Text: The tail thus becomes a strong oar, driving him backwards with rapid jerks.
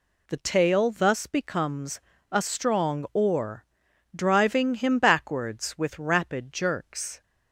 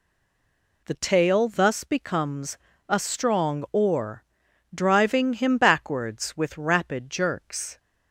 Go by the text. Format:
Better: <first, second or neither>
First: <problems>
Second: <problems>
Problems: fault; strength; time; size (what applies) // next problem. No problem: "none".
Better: first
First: pauses between "becomes" and "a"; slight; at 1.9 s; 0.32 s long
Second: stays silent before the first word; slight; until 0.8 s; 0.8 s long // pauses between "becomes" and "a"; slight; at 2.5 s; 0.32 s long